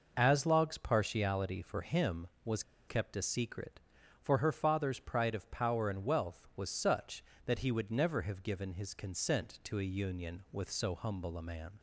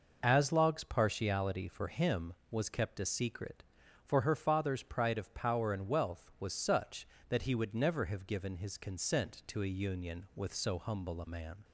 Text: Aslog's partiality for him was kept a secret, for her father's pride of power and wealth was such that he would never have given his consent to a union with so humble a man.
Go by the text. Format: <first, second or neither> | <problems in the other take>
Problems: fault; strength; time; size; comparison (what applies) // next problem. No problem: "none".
second | pauses between "was" and "kept"; slight; at 2.6 s; 0.25 s long